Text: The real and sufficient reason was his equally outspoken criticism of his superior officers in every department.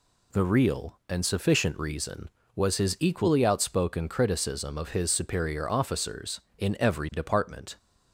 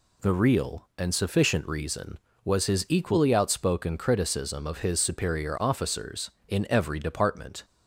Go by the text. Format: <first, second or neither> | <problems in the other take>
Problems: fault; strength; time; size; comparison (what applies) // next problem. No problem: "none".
neither | none